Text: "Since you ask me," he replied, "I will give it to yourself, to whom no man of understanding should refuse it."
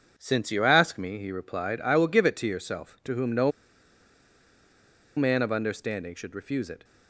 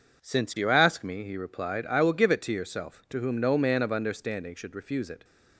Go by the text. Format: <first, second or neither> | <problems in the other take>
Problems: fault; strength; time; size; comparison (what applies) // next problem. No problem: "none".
second | pauses between "no" and "man"; strong; at 3.5 s; 1.6 s long